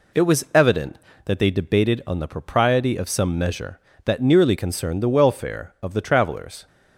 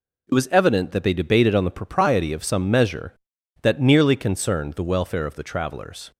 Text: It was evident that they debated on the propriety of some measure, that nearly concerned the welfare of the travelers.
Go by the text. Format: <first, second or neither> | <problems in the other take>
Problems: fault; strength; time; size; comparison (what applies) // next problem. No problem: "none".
neither | none